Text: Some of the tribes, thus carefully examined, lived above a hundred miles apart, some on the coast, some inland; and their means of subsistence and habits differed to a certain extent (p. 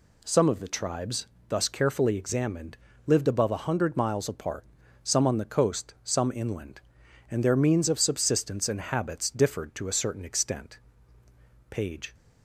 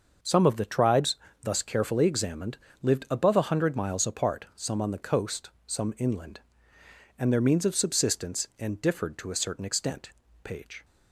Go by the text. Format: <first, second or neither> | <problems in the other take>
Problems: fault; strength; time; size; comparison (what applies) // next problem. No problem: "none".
first | starts louder than the rest; until 1.5 s; 6 dB // skips "habits"; at 8.8 s